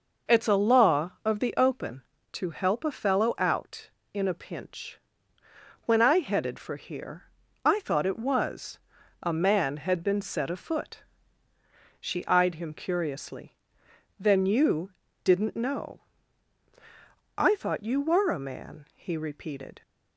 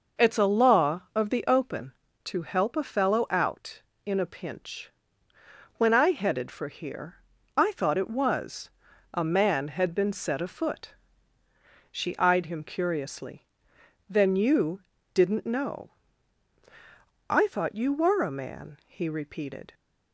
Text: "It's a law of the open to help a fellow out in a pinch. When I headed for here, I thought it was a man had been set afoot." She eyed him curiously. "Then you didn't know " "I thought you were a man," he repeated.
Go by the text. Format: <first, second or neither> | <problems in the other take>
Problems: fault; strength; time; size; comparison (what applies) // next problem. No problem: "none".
neither | pauses between "was" and "a"; the same in both // pauses between "you" and "didn't"; slight; the same in both